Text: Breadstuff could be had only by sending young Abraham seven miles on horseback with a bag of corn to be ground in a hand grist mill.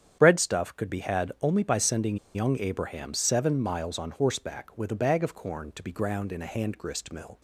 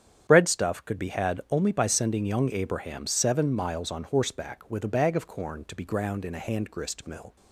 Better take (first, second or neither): second